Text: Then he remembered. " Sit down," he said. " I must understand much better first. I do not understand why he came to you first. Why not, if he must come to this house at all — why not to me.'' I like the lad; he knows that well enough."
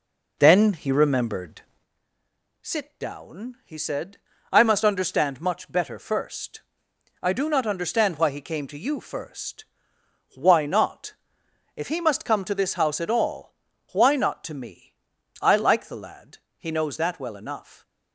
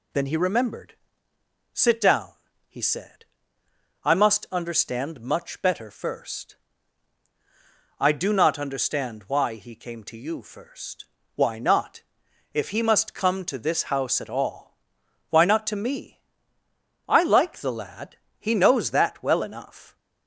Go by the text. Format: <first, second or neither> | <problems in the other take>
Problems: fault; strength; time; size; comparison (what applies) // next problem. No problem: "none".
second | starts louder than the rest; noticeable; until 1.9 s; 4 dB